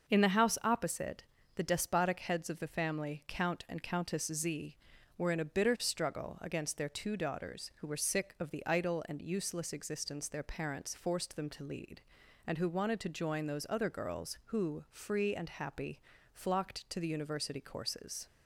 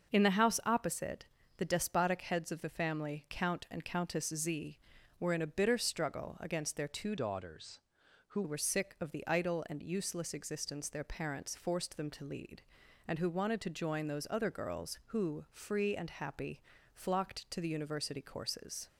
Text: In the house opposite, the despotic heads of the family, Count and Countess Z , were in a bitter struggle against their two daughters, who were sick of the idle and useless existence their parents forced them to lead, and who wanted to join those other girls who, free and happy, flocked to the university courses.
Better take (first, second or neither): first